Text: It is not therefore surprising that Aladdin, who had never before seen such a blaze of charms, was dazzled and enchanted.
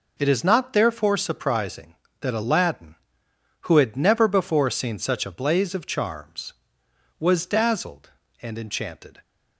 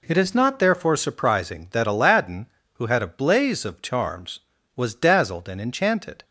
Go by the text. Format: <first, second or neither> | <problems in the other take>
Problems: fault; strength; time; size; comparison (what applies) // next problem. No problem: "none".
first | skips "never before seen such"; at 3.0 s